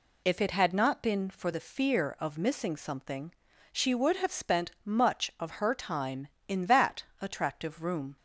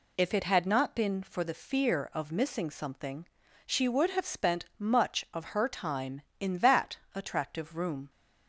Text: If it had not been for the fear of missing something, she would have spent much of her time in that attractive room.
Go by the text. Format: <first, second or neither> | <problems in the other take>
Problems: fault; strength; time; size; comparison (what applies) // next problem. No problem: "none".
neither | pauses between "that" and "attractive"; slight; the same in both